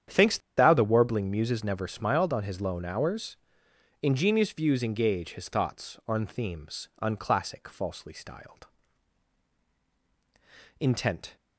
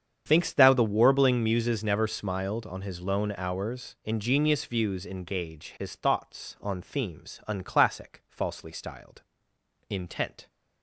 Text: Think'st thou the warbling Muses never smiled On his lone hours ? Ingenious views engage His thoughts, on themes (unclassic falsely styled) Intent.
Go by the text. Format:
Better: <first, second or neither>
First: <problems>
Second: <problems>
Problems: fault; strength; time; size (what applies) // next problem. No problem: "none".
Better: second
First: starts louder than the rest; strong; until 1.2 s; 9 dB // pauses between "Think'st" and "thou"; slight; at 0.3 s; 0.18 s long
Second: starts louder than the rest; strong; until 1.2 s; 8 dB